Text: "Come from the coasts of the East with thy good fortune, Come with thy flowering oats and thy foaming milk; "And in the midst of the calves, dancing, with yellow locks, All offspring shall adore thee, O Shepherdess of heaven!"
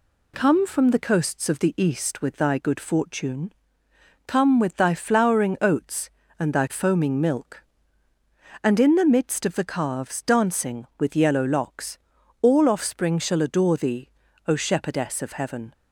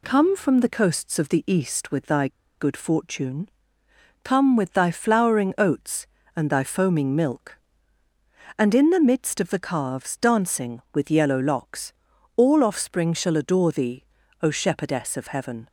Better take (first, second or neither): first